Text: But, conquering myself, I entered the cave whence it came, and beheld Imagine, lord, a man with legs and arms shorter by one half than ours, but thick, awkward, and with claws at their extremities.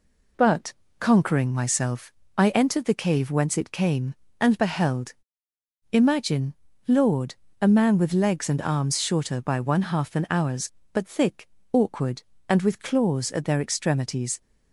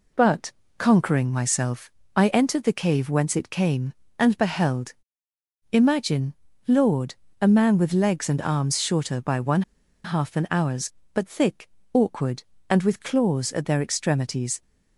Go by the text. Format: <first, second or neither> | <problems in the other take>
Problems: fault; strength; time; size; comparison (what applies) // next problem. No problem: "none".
first | pauses between "beheld" and "Imagine"; noticeable; at 4.9 s; 0.78 s long; noticeable in the first // pauses between "one" and "half"; at 9.6 s; 0.43 s long